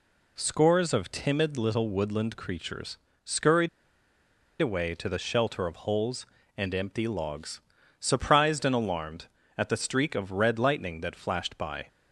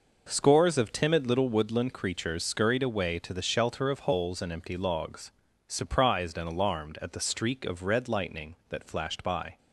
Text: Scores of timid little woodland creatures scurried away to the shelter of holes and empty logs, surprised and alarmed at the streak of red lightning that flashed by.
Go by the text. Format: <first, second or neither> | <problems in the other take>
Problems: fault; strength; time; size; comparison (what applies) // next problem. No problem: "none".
second | pauses between "creatures" and "scurried"; slight; at 2.9 s; 0.26 s long // pauses between "scurried" and "away"; noticeable; at 3.6 s; 0.92 s long